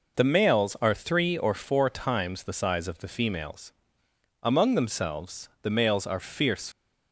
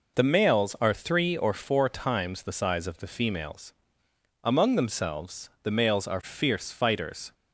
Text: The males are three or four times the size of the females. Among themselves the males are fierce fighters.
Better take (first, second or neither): second